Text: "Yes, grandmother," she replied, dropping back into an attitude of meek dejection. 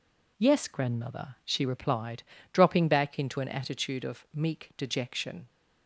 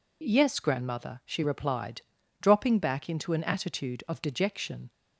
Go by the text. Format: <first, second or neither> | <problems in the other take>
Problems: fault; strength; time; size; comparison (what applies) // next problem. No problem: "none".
first | skips "meek"; at 4.2 s